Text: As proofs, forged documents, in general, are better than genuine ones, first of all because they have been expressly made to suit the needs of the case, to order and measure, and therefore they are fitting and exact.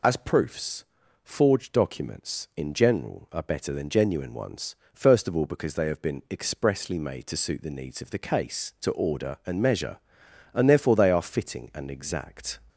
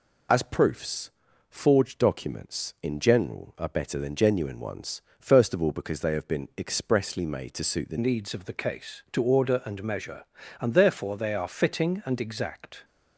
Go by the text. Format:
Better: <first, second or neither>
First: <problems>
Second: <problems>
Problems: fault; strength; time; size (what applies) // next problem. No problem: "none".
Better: first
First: none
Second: changes voice at "needs"; from 7.9 s on; 4.9 s long